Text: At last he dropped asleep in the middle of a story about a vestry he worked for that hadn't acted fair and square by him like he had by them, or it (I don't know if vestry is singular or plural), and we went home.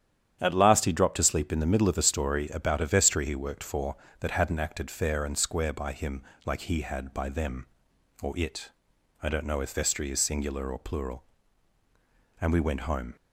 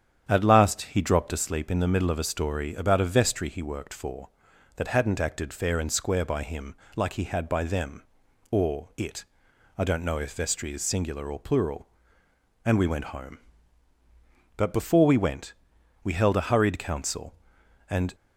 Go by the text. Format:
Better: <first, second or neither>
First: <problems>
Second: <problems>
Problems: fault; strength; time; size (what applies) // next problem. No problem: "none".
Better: first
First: starts louder than the rest; strong; until 1.4 s; 9.5 dB // pauses between "him" and "like"; slight; at 6.2 s; 0.24 s long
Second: starts louder than the rest; strong; until 1.2 s; 8.5 dB // pauses between "him" and "like"; slight; at 6.7 s; 0.22 s long // goes on to say "But before we went we held a hurried council and"; strong; from 14.5 s on; 3.5 s long